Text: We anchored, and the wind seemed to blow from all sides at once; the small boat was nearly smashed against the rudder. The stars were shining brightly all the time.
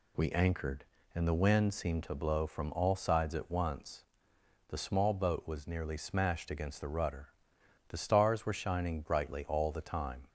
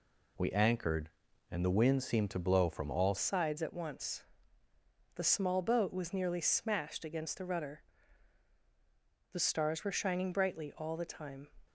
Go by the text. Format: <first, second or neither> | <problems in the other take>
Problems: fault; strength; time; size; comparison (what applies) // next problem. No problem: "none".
first | changes voice at "sides"; from 3.1 s on; 8.3 s long